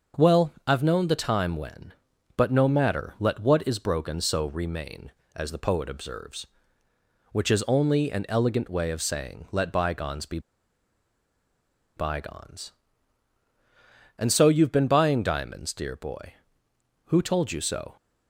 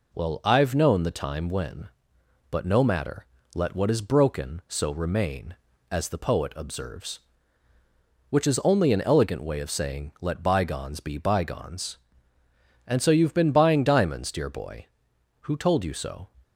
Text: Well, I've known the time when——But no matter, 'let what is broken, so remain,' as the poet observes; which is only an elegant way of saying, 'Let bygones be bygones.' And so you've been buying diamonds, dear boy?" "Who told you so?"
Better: second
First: pauses between "be" and "bygones"; strong; at 10.3 s; 1.5 s long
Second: none

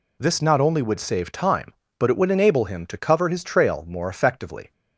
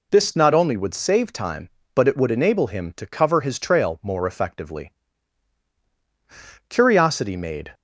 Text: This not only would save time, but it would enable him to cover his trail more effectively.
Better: first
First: none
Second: goes on to say "Curiosity made"; noticeable; from 6.6 s on; 1.0 s long

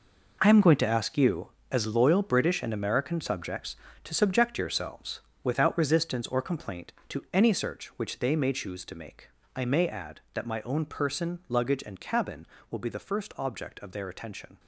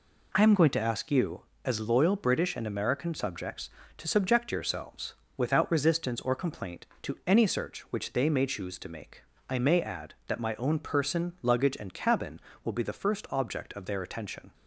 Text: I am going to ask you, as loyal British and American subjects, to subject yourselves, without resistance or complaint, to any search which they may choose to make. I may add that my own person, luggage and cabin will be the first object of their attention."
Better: second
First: gets quieter; strong; throughout; 11.5 dB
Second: none

